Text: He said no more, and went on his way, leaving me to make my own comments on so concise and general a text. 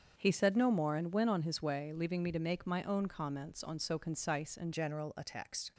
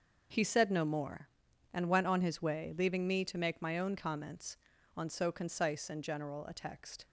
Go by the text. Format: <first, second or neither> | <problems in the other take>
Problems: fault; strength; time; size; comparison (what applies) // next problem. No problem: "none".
second | starts louder than the rest; until 1.1 s; 7 dB; also in the second // changes voice at "general"; from 4.7 s on; 1.0 s long